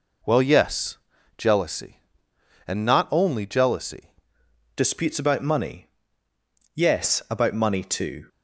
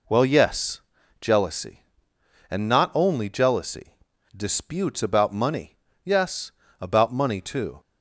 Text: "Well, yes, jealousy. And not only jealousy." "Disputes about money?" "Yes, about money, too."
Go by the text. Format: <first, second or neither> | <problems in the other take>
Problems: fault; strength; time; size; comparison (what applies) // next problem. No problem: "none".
second | changes voice at "Disputes"; from 4.7 s on; 3.5 s long